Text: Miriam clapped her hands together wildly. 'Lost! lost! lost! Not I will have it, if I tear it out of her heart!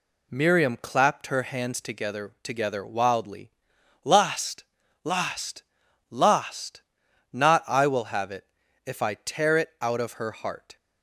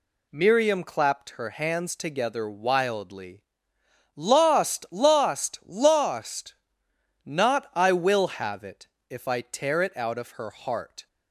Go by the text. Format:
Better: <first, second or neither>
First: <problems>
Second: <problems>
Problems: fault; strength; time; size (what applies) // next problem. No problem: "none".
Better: second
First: says "together" twice; at 2.4 s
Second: none